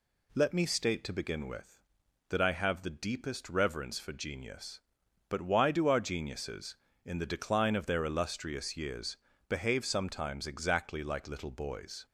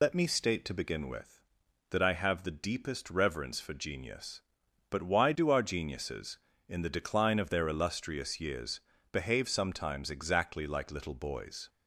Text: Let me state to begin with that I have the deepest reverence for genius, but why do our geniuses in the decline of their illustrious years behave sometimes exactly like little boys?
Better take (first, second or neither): first